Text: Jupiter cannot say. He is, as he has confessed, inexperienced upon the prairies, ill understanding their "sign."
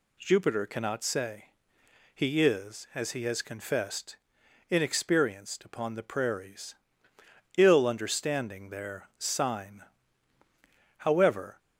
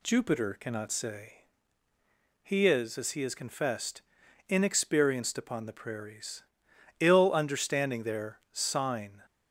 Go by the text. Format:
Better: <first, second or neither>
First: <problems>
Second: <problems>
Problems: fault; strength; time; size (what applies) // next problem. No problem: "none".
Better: second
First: goes on to say "However"; from 10.9 s on; 0.60 s long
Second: none